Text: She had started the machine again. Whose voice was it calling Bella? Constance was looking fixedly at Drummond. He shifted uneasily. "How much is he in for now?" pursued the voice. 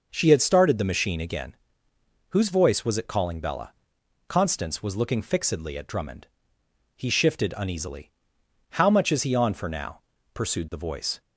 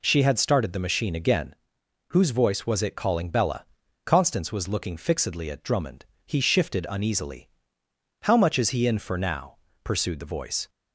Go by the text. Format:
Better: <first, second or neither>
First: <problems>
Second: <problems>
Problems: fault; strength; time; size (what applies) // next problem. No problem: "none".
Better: second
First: says "on" for "in"; at 9.3 s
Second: none